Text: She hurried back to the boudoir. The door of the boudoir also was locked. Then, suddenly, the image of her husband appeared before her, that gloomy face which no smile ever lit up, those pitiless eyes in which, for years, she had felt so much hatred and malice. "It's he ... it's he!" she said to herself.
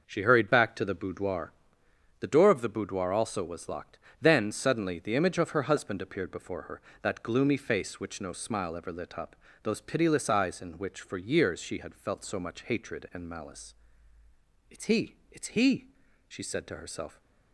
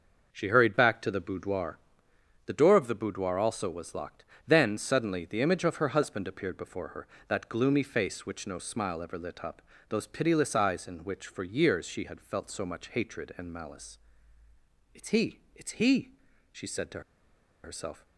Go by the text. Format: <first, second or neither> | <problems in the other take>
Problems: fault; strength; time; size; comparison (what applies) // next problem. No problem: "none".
first | starts louder than the rest; until 1.3 s; 6 dB; also in the first // pauses between "to" and "herself"; noticeable; at 17.0 s; 0.63 s long